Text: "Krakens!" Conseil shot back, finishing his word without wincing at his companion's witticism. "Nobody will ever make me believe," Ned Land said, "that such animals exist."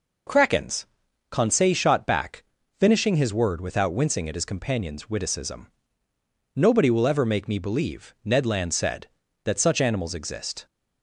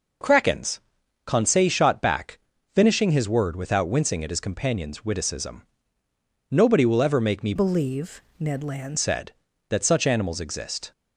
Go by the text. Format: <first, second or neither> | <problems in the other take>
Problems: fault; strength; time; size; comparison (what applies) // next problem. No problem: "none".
first | changes voice from "believe" to "Land"; from 7.5 to 8.9 s; 1.4 s long